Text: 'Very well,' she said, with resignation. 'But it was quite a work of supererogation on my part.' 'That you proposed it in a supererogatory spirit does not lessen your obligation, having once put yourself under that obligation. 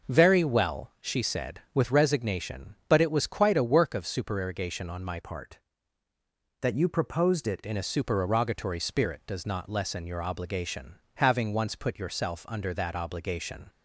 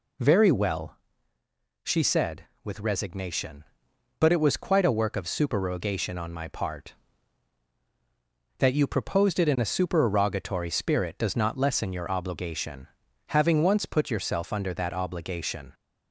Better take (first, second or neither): second